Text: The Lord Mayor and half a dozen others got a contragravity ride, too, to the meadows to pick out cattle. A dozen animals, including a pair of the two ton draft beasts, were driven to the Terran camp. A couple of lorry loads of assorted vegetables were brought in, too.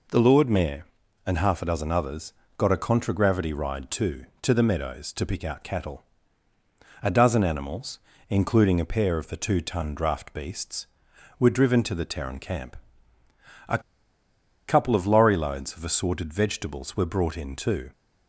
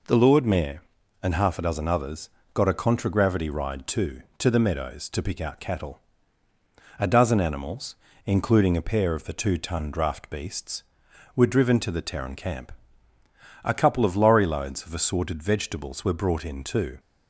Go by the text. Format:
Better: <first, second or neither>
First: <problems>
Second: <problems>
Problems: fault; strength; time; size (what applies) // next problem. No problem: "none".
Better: second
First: pauses between "others" and "got"; slight; at 2.3 s; 0.26 s long // pauses between "A" and "couple"; noticeable; at 13.7 s; 0.89 s long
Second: pauses between "others" and "got"; slight; at 2.2 s; 0.26 s long